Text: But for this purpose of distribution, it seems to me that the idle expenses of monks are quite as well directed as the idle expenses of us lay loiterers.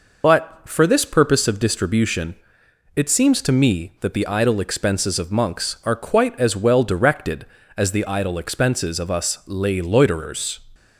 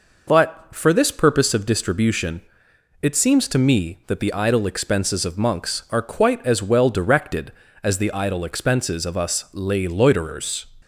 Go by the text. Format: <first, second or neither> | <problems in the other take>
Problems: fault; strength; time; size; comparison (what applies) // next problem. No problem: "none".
second | loses the start of "But"; at 0.2 s; 30 ms